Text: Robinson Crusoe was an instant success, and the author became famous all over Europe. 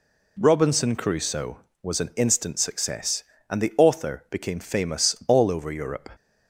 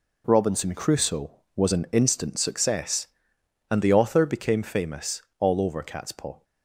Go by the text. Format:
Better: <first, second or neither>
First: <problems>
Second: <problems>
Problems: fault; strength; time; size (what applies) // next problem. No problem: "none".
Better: first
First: none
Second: pauses between "famous" and "all"; slight; at 5.2 s; 0.16 s long // says "Catspaw" for "Europe"; at 5.8 s